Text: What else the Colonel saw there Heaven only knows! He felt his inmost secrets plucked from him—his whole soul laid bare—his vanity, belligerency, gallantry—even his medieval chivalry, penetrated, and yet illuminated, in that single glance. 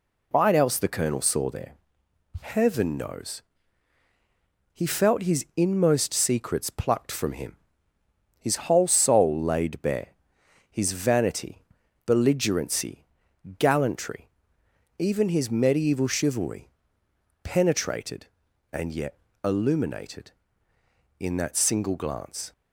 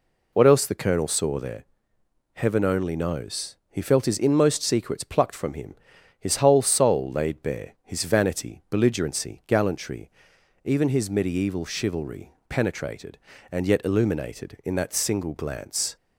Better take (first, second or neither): second